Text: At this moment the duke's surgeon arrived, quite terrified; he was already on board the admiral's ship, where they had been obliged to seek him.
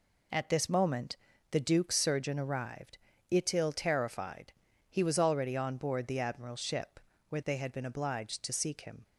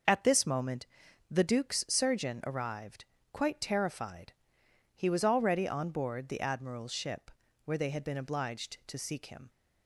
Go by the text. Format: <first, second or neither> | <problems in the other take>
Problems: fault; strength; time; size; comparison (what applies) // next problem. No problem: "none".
second | pauses between "moment" and "the"; slight; at 1.1 s; 0.36 s long; also in the second // says "itil" for "quite"; at 3.3 s